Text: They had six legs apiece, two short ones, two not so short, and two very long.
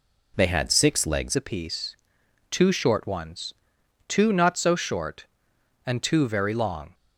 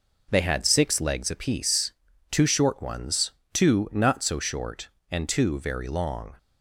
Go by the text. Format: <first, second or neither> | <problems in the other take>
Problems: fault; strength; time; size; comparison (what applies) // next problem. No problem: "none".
second | changes voice at "apiece"; from 1.3 s on; 5.6 s long